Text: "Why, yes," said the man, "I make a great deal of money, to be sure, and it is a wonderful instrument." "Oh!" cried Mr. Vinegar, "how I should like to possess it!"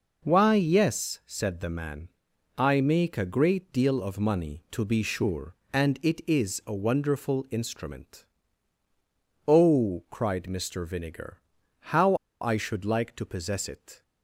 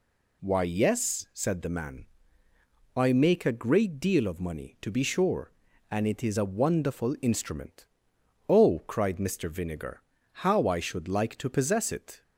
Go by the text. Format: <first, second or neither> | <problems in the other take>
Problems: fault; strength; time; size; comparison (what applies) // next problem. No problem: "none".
second | pauses between "how" and "I"; slight; at 12.1 s; 0.26 s long